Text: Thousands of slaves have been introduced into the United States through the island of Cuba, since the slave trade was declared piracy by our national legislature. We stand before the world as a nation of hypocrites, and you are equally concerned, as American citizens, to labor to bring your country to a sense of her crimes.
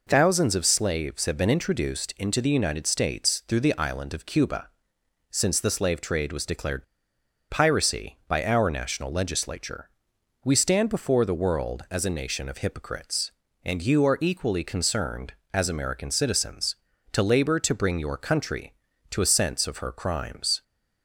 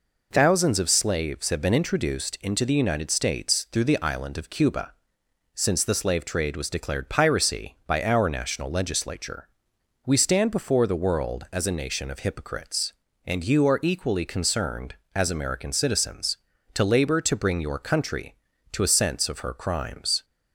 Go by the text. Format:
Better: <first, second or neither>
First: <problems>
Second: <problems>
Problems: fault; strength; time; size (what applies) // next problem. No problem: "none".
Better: second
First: pauses between "declared" and "piracy"; noticeable; at 6.8 s; 0.65 s long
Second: none